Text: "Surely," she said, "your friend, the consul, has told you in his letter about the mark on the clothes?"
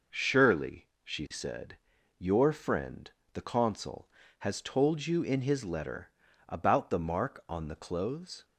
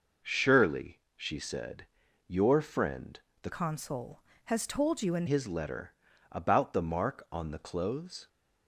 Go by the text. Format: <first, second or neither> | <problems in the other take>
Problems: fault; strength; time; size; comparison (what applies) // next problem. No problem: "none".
first | changes voice from "consul" to "in"; from 3.5 to 5.2 s; 1.7 s long // pauses between "letter" and "about"; at 5.9 s; 0.38 s long; also in the first